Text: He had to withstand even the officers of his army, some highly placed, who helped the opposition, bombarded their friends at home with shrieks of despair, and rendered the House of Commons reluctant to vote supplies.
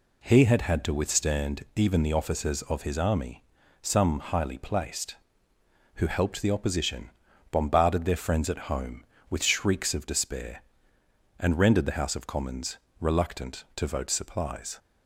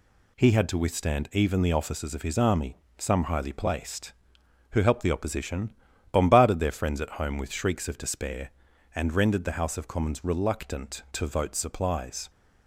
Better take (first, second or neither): second